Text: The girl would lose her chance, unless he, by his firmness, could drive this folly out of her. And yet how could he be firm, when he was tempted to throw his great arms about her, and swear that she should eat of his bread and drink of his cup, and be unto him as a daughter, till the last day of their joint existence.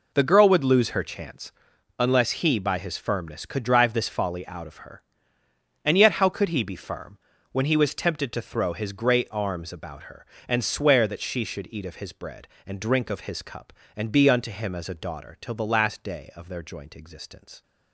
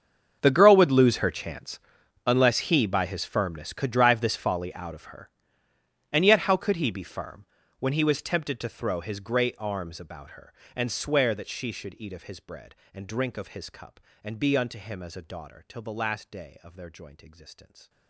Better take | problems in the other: first | gets quieter; strong; throughout; 21 dB

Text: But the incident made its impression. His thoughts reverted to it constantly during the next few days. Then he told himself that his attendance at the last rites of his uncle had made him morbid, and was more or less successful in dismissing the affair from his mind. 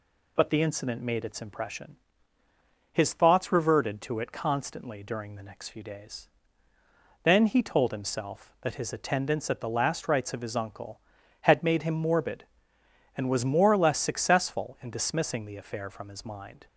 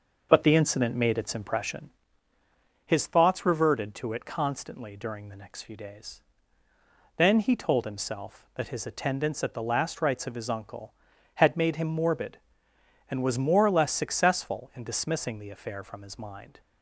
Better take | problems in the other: first | starts louder than the rest; noticeable; until 2.1 s; 6 dB

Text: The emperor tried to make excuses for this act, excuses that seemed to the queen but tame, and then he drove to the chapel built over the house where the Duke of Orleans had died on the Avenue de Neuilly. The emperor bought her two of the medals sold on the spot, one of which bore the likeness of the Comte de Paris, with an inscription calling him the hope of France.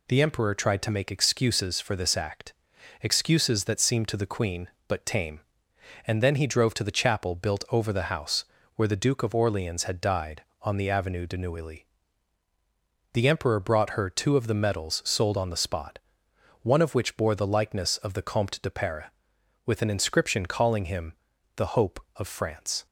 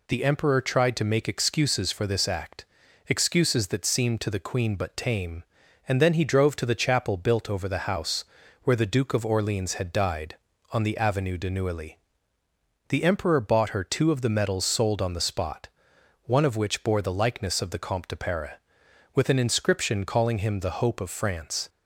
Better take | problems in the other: second | pauses between "house" and "where"; slight; at 8.4 s; 0.32 s long; also in the second // says "brought" for "bought"; at 13.5 s // pauses between "him" and "the"; at 21.1 s; 0.42 s long

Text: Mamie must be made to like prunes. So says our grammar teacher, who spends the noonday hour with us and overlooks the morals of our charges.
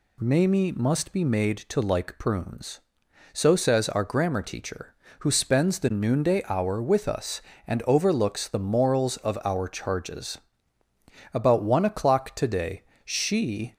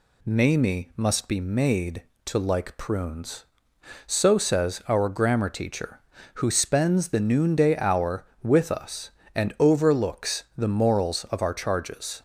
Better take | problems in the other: second | goes on to say "About one o'clock today she"; strong; from 11.3 s on; 2.4 s long

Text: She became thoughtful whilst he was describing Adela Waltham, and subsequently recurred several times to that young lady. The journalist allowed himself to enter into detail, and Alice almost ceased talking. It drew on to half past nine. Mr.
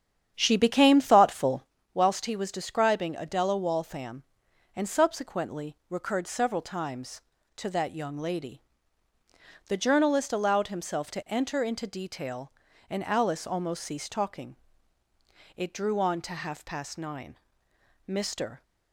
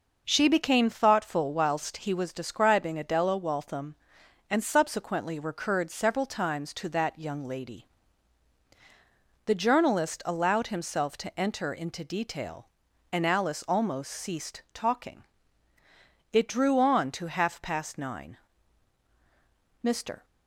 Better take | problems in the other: second | starts louder than the rest; strong; until 1.8 s; 8.5 dB // pauses between "thoughtful" and "whilst"; slight; at 1.6 s; 0.30 s long

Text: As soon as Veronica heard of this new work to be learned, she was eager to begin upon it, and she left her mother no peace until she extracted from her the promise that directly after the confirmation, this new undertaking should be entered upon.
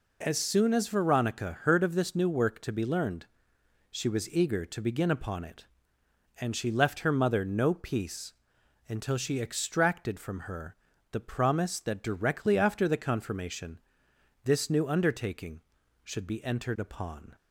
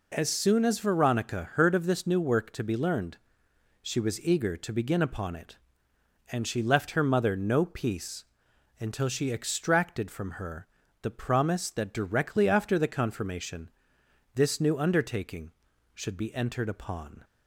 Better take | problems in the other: neither | pauses between "peace" and "until"; noticeable; the same in both // pauses between "her" and "the"; slight; the same in both

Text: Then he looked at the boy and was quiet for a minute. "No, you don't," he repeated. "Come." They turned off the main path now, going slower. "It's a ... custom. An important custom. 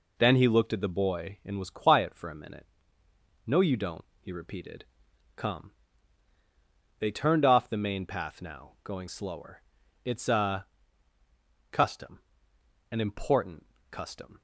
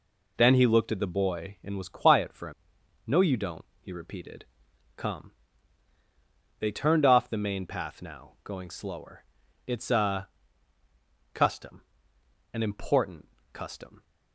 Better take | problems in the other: first | skips "minute"; at 2.7 s // pauses between "important" and "custom"; slight; at 13.2 s; 0.24 s long; slight in the first

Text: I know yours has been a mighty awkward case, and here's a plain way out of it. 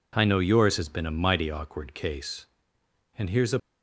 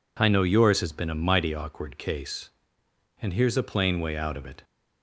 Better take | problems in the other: second | stops before "plain way out of it"; at 3.5 s

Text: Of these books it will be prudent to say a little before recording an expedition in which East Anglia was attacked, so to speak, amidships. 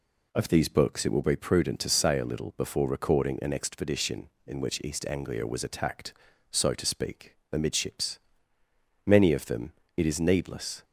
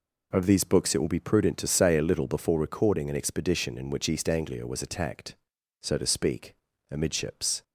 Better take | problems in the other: second | goes on to say "Many of them it is needless"; strong; from 9.0 s on; 1.7 s long

